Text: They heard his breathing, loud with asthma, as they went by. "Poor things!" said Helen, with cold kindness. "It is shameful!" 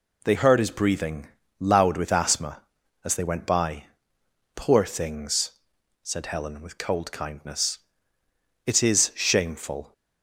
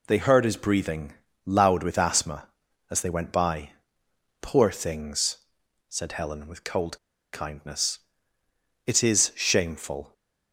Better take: first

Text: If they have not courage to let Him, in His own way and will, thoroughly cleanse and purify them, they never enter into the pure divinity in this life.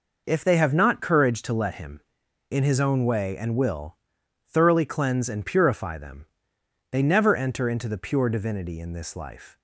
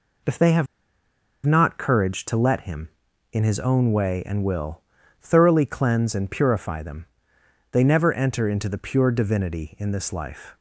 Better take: first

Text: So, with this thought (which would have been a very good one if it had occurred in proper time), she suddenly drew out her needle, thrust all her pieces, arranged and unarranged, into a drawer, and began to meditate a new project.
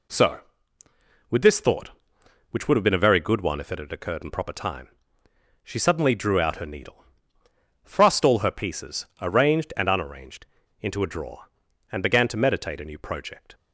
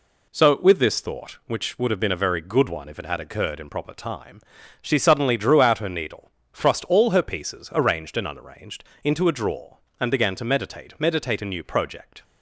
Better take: first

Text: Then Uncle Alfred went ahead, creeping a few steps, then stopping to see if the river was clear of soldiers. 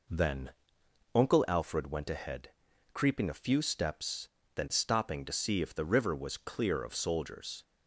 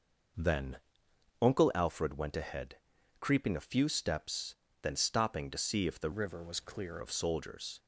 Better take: first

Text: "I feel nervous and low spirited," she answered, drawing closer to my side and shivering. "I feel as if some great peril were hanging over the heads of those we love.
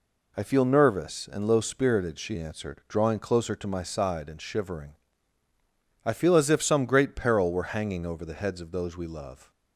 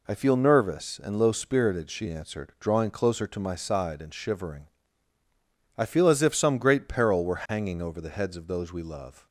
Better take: neither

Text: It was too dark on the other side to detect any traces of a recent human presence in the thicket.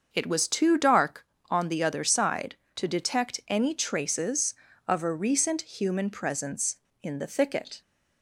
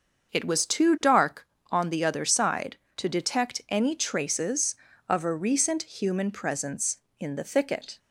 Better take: neither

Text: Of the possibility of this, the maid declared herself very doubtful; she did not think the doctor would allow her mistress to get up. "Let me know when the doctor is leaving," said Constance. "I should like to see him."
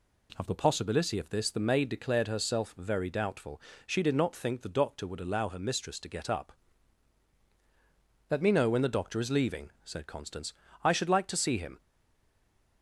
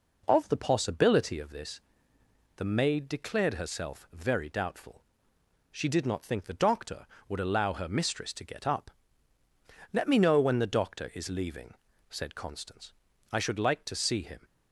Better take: second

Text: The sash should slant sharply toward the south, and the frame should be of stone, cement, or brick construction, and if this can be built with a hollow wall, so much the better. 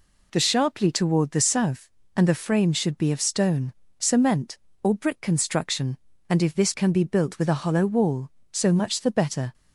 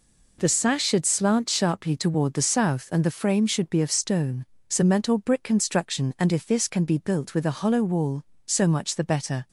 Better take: second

